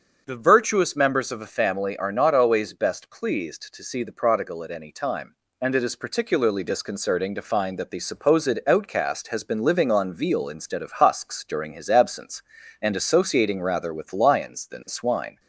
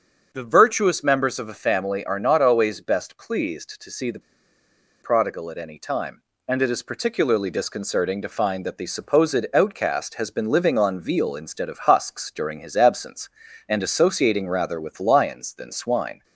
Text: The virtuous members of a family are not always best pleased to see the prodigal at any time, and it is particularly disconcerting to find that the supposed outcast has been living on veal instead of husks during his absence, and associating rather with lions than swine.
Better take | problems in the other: first | starts louder than the rest; strong; until 1.3 s; 7 dB; strong in the first // pauses between "the" and "prodigal"; noticeable; at 4.1 s; 0.82 s long

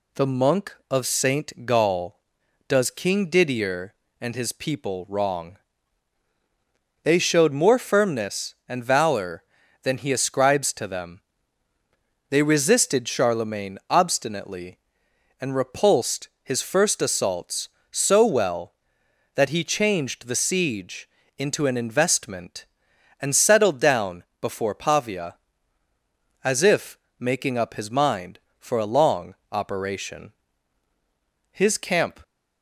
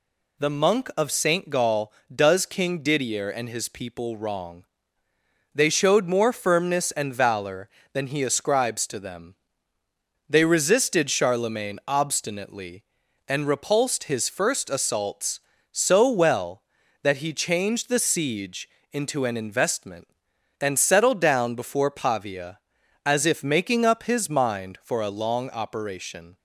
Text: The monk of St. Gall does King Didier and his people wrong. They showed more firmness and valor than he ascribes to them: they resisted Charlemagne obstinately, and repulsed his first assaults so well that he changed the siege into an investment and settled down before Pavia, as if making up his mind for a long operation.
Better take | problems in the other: second | pauses between "repulsed" and "his"; slight; at 16.2 s; 0.16 s long // pauses between "siege" and "into"; slight; at 21.0 s; 0.30 s long; slight in the second // pauses between "down" and "before"; slight; at 24.2 s; 0.16 s long // pauses between "if" and "making"; slight; at 26.9 s; 0.18 s long // pauses between "long" and "operation"; slight; at 29.3 s; 0.18 s long // goes on to say "His camp"; noticeable; from 31.5 s on; 0.70 s long

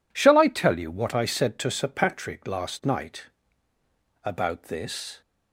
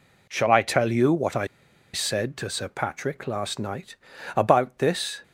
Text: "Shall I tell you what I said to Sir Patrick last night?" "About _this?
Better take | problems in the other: first | pauses between "I" and "said"; noticeable; at 1.4 s; 0.46 s long

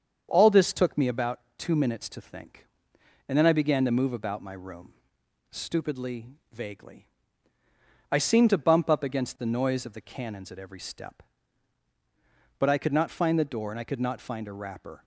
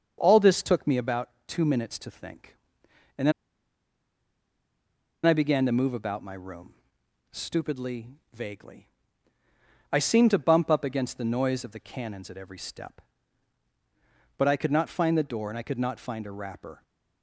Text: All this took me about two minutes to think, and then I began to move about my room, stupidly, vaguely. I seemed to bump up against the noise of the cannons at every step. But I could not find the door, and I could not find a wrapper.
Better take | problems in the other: first | starts louder than the rest; strong; until 1.2 s; 7 dB; strong in the first // pauses between "about" and "two"; slight; at 1.2 s; 0.18 s long; slight in the first // pauses between "then" and "I"; strong; at 3.3 s; 1.9 s long

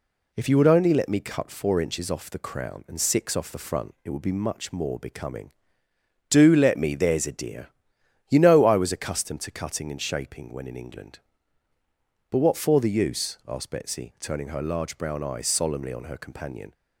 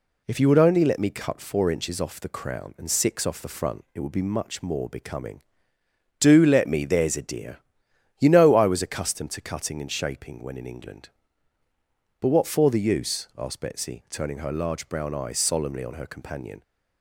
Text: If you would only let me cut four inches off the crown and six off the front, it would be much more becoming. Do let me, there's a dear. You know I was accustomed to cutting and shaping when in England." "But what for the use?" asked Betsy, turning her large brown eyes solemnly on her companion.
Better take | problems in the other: neither | none

